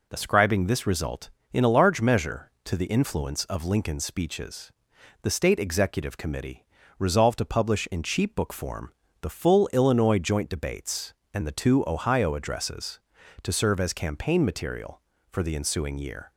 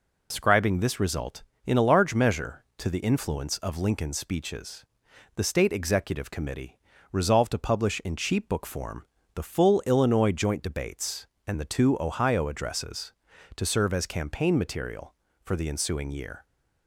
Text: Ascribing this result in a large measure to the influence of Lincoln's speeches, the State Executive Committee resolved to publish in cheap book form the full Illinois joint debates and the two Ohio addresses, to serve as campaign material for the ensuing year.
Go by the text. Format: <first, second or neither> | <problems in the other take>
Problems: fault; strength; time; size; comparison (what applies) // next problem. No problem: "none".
first | loses the start of "Ascribing"; at 0.3 s; 75 ms // pauses between "Committee" and "resolved"; slight; at 6.7 s; 0.34 s long; slight in the first // pauses between "form" and "the"; slight; at 9.0 s; 0.30 s long; slight in the first